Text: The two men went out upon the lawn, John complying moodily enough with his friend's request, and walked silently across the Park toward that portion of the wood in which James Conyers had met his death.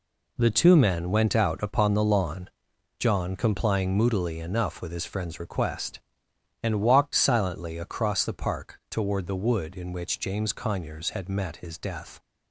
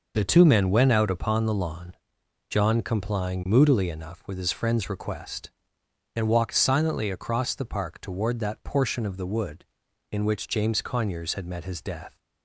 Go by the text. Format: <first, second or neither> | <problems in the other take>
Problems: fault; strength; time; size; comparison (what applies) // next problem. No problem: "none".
second | skips "that portion of"; at 9.2 s